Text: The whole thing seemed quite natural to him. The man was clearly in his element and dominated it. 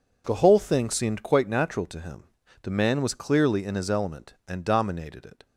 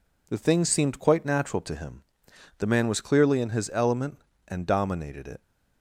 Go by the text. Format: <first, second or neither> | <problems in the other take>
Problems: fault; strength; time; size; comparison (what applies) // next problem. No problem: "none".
first | skips "whole"; at 0.3 s